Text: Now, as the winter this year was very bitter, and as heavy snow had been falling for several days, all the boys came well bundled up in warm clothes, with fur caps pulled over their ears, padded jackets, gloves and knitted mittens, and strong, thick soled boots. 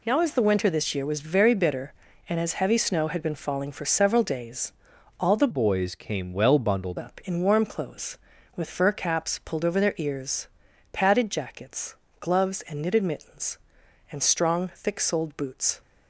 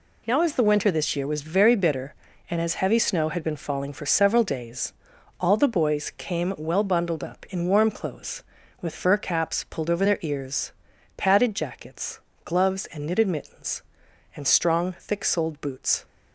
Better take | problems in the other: second | changes voice from "boys" to "bundled"; from 5.5 to 6.9 s; 1.4 s long

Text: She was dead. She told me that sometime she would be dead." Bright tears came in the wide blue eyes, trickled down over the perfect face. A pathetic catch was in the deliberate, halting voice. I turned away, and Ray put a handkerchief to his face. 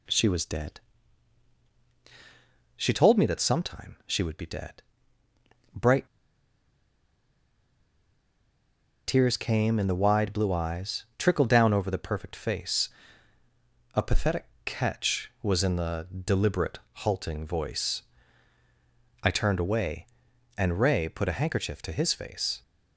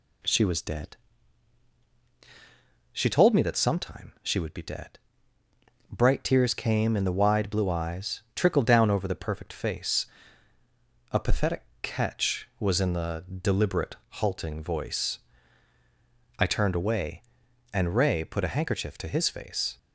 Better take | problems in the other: second | pauses between "Bright" and "tears"; strong; at 6.0 s; 3.0 s long // pauses between "pathetic" and "catch"; slight; at 14.4 s; 0.20 s long; slight in the second // pauses between "the" and "deliberate"; slight; at 16.0 s; 0.20 s long; slight in the second

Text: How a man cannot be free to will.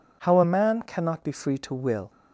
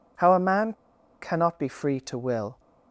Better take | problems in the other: first | pauses between "man" and "cannot"; noticeable; at 0.7 s; 0.48 s long

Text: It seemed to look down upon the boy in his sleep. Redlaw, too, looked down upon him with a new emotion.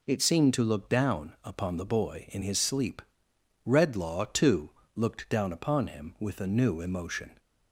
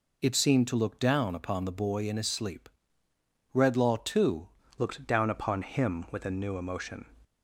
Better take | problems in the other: first | changes voice at "looked"; from 4.7 s on; 2.3 s long

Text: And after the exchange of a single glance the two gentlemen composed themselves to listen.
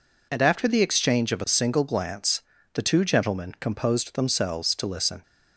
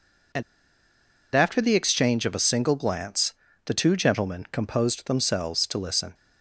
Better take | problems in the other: first | pauses between "And" and "after"; noticeable; at 0.4 s; 0.92 s long // pauses between "glance" and "the"; slight; at 3.3 s; 0.32 s long; slight in the first

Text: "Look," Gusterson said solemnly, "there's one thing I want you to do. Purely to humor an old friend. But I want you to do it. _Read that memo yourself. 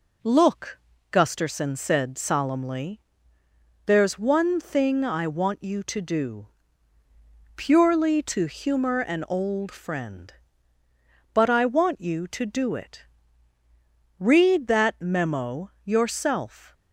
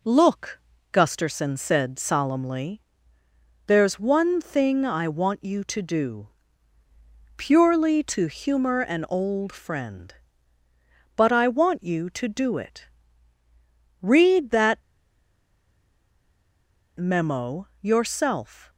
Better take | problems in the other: first | pauses between "that" and "memo"; strong; at 14.7 s; 2.1 s long // pauses between "memo" and "yourself"; slight; at 17.6 s; 0.16 s long; slight in the first

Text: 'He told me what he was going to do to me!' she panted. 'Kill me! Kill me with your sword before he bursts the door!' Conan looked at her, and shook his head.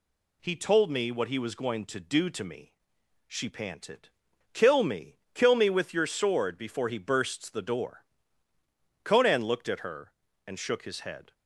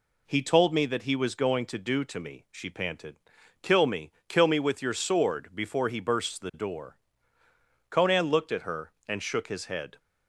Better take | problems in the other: first | says "that" for "what"; at 0.8 s

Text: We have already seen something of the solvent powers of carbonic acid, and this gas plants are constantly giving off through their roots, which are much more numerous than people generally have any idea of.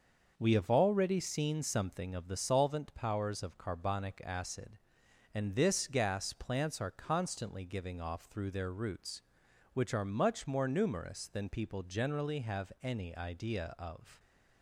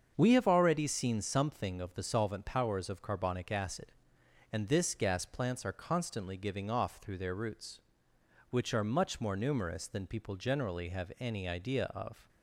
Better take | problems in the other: neither | starts louder than the rest; the same in both

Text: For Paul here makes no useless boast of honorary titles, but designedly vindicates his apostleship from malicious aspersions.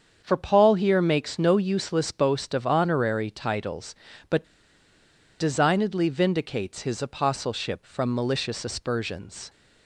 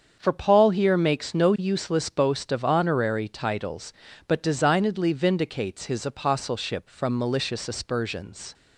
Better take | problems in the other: second | starts louder than the rest; strong; until 1.2 s; 7 dB; strong in the second // pauses between "but" and "designedly"; noticeable; at 4.4 s; 0.94 s long

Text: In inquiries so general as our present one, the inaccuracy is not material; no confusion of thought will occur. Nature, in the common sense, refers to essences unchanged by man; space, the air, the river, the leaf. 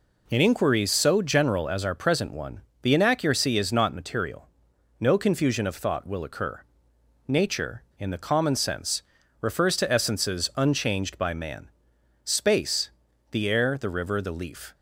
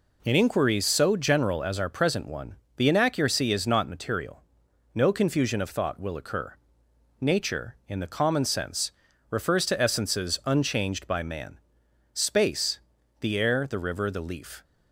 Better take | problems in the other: neither | none

